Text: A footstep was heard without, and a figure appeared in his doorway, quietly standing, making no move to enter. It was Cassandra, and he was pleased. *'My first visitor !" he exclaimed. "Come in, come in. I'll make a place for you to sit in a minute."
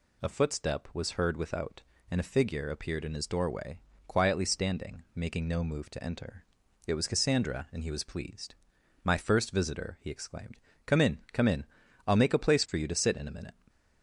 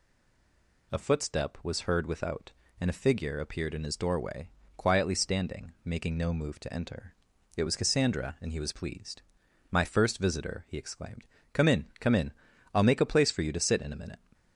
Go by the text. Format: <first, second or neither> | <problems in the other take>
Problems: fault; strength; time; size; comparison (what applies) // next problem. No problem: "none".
first | stays silent before the first word; slight; until 0.9 s; 0.9 s long